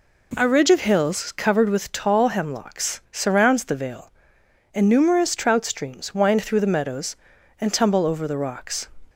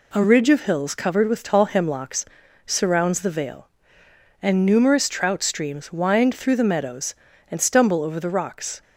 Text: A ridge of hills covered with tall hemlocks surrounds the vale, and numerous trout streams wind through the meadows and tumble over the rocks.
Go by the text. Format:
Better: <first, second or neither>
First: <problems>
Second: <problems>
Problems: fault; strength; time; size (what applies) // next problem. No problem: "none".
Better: first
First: none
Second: pauses between "hemlocks" and "surrounds"; at 2.2 s; 0.40 s long // says "stumble" for "tumble"; at 7.6 s